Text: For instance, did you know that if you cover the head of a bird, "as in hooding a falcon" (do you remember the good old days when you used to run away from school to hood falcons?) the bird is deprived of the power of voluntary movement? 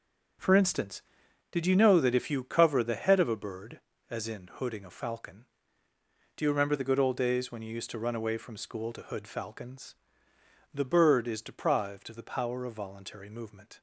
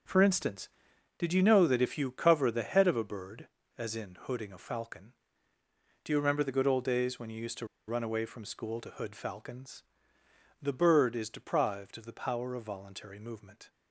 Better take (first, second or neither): first